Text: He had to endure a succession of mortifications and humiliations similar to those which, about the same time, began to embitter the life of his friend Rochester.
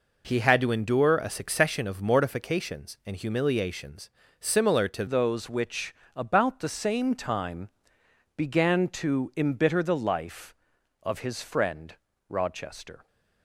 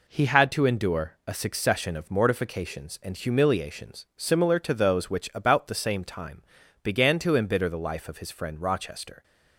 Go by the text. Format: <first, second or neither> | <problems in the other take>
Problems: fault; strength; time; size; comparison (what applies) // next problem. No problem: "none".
second | pauses between "humiliations" and "similar"; slight; at 4.0 s; 0.30 s long // changes voice at "those"; from 5.0 s on; 8.0 s long // pauses between "friend" and "Rochester"; slight; at 11.9 s; 0.34 s long